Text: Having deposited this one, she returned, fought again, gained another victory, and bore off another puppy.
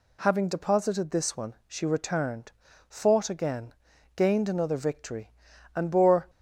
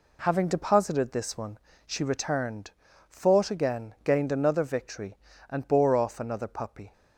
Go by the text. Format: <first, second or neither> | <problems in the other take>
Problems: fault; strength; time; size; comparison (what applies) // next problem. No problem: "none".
second | stops before "off another puppy"; at 6.2 s